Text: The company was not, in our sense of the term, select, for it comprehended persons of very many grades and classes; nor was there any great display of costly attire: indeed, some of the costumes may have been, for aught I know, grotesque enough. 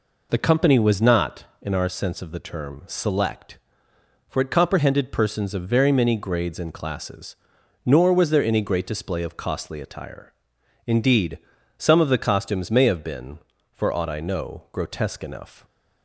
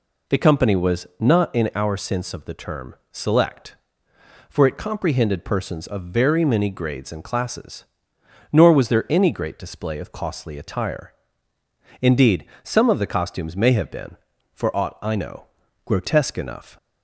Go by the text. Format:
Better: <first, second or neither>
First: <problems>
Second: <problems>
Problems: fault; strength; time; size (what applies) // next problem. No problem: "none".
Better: neither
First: none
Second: none